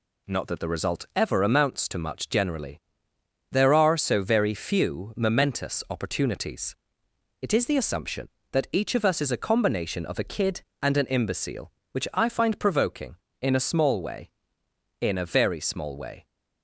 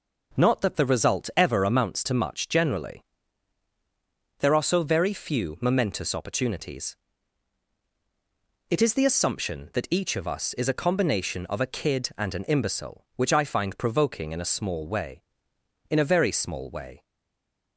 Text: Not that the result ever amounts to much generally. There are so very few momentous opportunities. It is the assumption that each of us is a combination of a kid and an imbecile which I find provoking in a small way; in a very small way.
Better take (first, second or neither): first